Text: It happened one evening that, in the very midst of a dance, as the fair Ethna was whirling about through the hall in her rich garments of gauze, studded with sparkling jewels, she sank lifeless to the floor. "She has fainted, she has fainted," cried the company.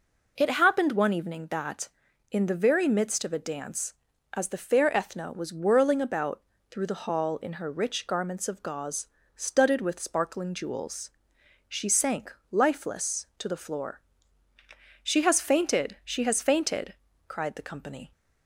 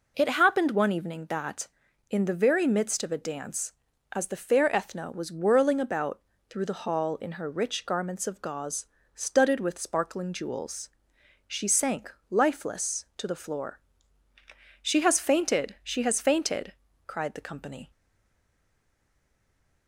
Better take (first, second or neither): first